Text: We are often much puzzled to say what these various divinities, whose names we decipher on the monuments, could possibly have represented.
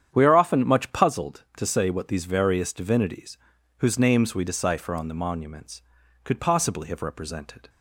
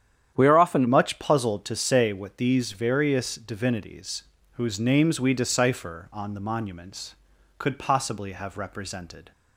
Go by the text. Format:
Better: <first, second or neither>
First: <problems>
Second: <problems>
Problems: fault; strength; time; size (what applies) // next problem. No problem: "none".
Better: first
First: starts louder than the rest; strong; until 1.1 s; 9 dB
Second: starts louder than the rest; strong; until 1.3 s; 9.5 dB // changes voice at "much"; from 0.8 s on; 8.5 s long